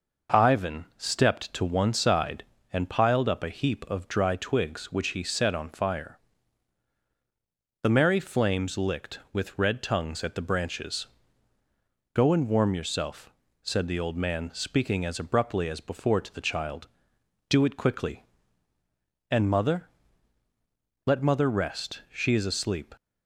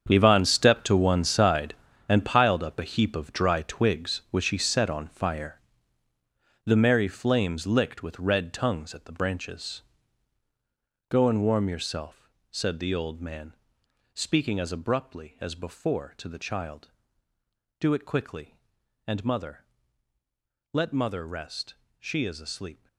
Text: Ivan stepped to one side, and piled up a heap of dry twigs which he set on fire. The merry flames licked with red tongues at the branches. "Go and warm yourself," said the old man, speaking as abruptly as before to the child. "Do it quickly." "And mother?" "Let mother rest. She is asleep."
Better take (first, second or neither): first